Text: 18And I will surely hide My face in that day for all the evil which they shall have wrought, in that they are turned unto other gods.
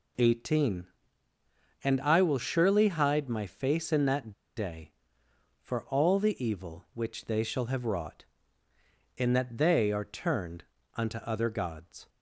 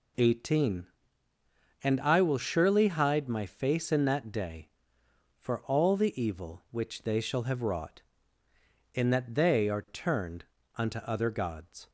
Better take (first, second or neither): second